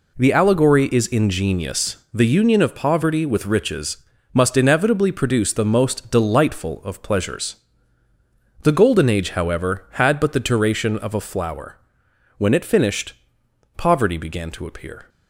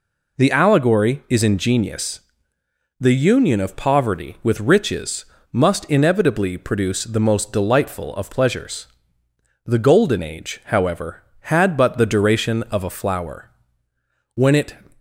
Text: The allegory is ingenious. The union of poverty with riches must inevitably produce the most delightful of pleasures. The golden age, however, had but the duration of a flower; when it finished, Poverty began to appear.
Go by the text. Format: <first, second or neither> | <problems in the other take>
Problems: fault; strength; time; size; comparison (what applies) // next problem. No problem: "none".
first | pauses between "riches" and "must"; slight; at 5.2 s; 0.26 s long; slight in the first // stops before "finished Poverty began to appear"; at 14.9 s